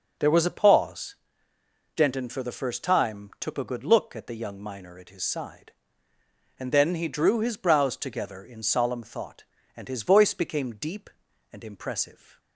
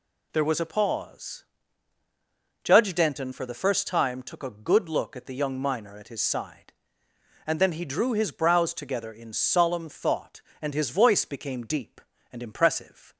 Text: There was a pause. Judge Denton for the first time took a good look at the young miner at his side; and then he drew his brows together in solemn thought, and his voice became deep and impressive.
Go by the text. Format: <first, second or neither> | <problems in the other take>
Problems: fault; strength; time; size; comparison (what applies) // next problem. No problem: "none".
second | skips "Judge"; at 1.5 s